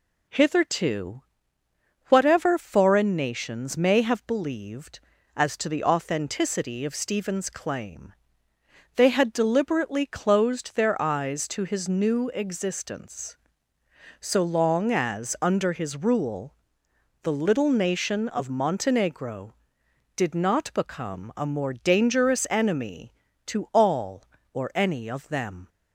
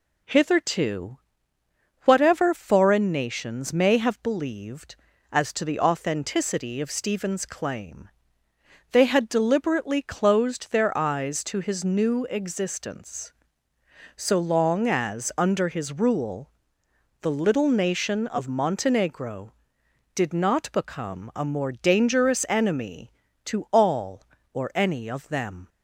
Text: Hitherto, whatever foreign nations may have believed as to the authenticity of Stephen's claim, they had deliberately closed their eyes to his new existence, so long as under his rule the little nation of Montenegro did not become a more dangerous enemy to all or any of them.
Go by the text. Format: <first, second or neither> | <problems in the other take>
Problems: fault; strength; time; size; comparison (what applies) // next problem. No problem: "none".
neither | pauses between "rule" and "the"; noticeable; the same in both